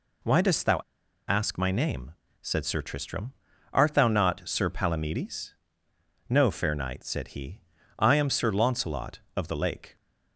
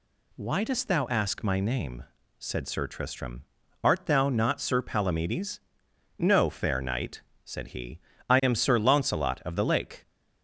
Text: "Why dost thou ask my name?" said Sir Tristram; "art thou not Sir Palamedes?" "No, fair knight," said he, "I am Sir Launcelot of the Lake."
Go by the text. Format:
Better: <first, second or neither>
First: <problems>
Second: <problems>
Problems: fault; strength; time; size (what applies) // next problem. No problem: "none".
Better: second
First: pauses between "thou" and "ask"; noticeable; at 0.7 s; 0.48 s long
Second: none